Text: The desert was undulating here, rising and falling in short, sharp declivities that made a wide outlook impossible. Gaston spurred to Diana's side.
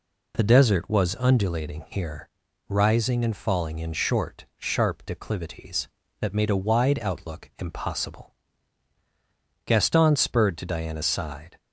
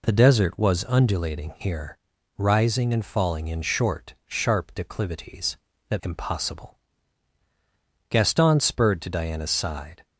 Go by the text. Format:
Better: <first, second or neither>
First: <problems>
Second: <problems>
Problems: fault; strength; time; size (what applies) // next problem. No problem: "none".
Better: first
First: none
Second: skips "made a wide outlook"; at 6.0 s